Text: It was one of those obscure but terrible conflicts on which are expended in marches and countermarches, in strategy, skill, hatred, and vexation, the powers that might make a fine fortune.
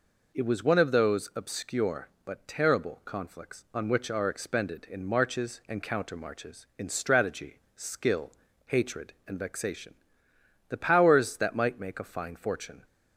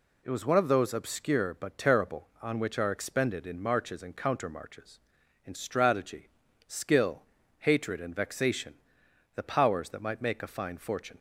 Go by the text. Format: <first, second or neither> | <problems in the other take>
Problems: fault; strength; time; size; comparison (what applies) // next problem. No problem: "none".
first | skips "conflicts"; at 2.3 s